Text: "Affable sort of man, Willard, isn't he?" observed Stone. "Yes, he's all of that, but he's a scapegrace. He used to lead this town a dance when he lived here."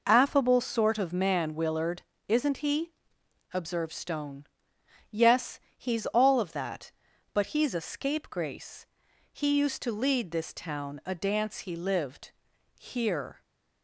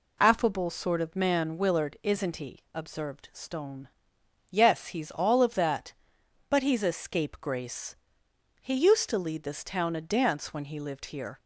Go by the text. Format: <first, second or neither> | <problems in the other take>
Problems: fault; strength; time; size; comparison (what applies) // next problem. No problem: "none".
second | skips "when"; at 11.5 s // pauses between "lived" and "here"; at 12.3 s; 0.42 s long